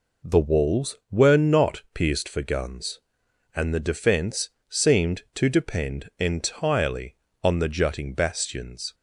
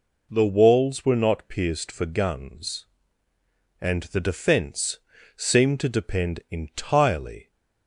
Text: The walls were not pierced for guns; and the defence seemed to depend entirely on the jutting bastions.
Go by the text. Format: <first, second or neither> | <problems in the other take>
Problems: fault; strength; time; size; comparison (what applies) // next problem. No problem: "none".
first | pauses between "defence" and "seemed"; at 4.9 s; 0.40 s long; slight in the first // stops before "on the jutting bastions"; at 7.5 s